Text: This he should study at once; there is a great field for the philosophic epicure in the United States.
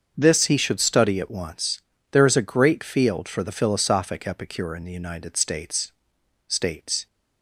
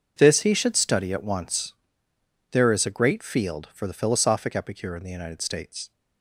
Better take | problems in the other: second | starts louder than the rest; until 1.1 s; 6.5 dB // says "States" twice; at 6.4 s

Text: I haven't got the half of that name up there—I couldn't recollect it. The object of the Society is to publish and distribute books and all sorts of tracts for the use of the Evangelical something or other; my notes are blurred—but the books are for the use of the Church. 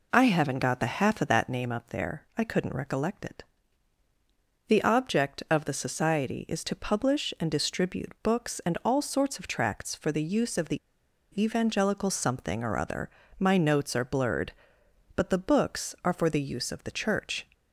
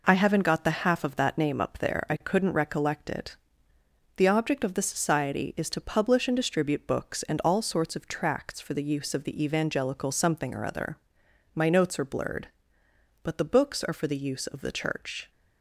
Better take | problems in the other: second | pauses between "the" and "Evangelical"; noticeable; at 10.7 s; 0.62 s long

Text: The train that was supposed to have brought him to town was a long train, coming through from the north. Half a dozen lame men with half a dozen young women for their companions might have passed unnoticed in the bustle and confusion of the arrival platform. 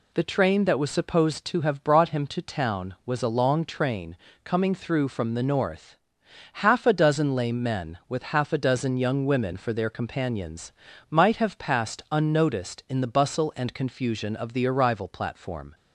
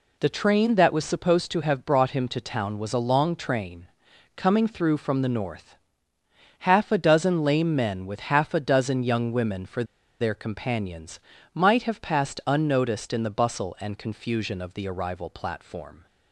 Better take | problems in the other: first | pauses between "for" and "their"; at 9.8 s; 0.36 s long // pauses between "companions" and "might"; slight; at 11.2 s; 0.34 s long; also in the first

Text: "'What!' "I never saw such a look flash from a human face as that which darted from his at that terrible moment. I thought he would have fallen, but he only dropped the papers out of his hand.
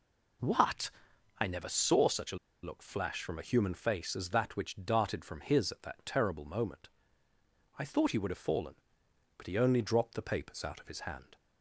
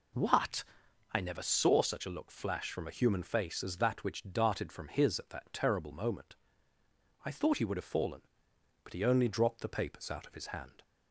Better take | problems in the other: second | pauses between "a" and "look"; slight; at 2.3 s; 0.26 s long

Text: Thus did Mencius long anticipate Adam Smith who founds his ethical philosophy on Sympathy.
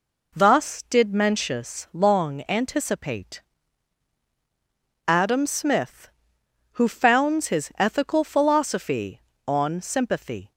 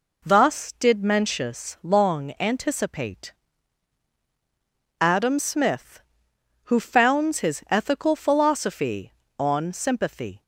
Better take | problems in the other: neither | pauses between "anticipate" and "Adam"; strong; the same in both

